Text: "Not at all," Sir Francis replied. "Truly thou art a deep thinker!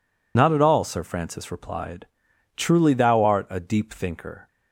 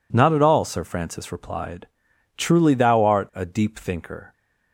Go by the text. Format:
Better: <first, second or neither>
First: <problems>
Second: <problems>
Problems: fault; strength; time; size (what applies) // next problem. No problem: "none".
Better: second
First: loses the start of "Not"; at 0.3 s; 55 ms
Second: none